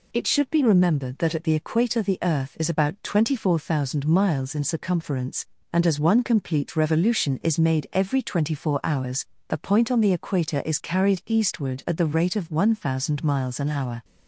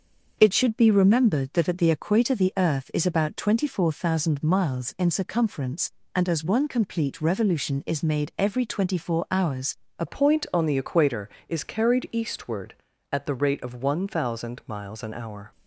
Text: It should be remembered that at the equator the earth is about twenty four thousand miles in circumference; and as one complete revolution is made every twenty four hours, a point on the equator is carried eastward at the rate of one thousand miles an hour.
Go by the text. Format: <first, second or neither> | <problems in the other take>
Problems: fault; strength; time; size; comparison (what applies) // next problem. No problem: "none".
first | starts louder than the rest; until 1.4 s; 6 dB // changes voice at "point"; from 10.0 s on; 5.5 s long